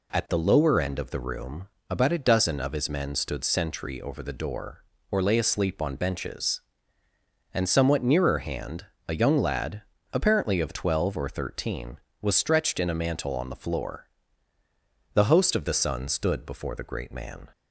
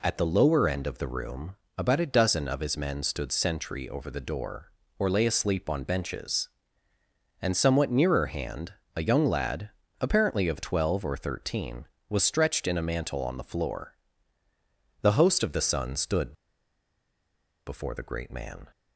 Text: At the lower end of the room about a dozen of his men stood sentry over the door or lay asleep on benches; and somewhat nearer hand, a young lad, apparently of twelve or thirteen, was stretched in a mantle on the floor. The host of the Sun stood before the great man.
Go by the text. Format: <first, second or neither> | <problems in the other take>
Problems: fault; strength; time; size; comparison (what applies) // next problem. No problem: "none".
first | pauses between "room" and "about"; slight; at 1.5 s; 0.22 s long; slight in the first // pauses between "stood" and "before"; strong; at 16.3 s; 1.3 s long